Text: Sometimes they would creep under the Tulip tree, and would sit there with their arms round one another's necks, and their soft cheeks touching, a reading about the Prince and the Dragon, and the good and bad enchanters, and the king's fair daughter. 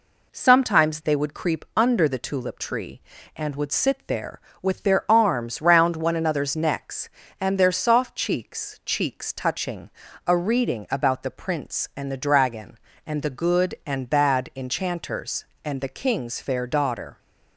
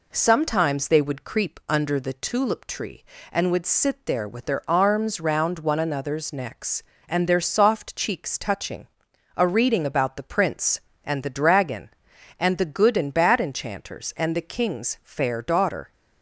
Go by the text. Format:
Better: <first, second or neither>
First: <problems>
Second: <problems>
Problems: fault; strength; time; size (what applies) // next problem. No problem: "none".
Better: second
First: says "cheeks" twice; at 8.8 s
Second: none